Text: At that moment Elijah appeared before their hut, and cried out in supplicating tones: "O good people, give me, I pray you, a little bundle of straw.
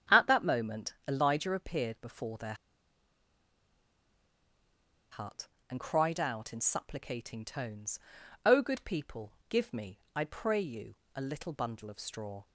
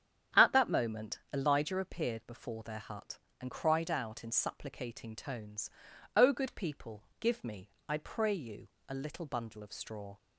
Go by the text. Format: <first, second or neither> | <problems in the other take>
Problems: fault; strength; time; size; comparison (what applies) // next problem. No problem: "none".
second | starts louder than the rest; strong; until 1.2 s; 8.5 dB; strong in the second // pauses between "their" and "hut"; strong; at 2.5 s; 2.5 s long